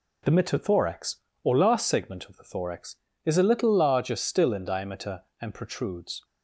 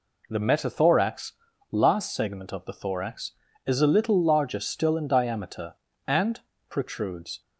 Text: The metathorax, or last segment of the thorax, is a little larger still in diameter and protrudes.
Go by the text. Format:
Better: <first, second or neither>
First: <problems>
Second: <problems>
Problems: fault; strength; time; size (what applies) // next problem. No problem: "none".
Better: first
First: none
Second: skips "or"; at 1.5 s // pauses between "and" and "protrudes"; slight; at 6.4 s; 0.30 s long